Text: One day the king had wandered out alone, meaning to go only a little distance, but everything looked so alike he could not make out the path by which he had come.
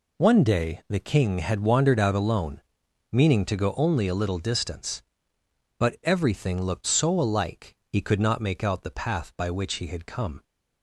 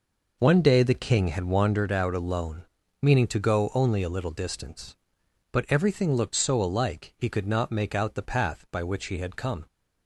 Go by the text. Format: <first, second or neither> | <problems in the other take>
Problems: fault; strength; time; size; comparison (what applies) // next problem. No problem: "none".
first | starts louder than the rest; noticeable; until 1.9 s; 5 dB